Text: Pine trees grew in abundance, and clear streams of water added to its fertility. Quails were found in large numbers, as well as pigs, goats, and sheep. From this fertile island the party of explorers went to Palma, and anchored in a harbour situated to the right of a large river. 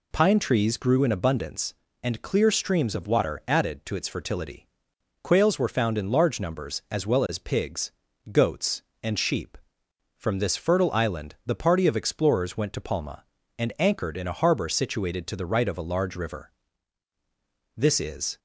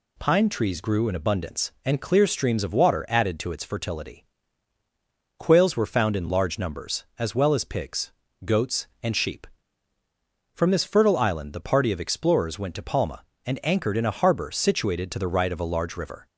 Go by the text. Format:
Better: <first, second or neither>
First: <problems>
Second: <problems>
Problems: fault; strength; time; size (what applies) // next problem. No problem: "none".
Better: second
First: goes on to say "This is"; noticeable; from 17.7 s on; 0.62 s long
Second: none